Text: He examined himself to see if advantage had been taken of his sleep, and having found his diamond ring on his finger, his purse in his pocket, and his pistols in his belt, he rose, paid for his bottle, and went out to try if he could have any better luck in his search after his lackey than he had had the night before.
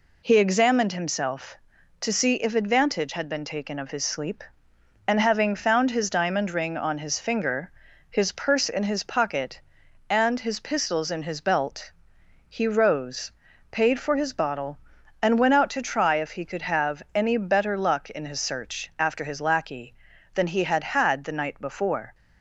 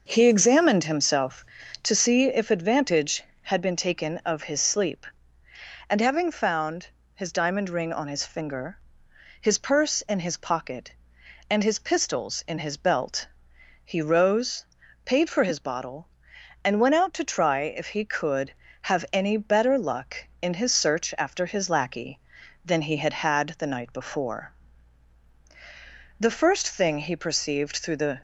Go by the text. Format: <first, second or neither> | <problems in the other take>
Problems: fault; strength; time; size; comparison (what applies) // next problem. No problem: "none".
first | pauses between "found" and "his"; slight; at 6.8 s; 0.26 s long // goes on to say "The first thing he perceived through the"; strong; from 26.2 s on; 2.0 s long